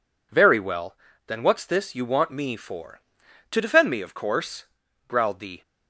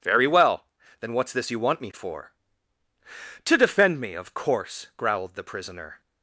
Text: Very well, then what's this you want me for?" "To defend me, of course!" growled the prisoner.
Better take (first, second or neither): second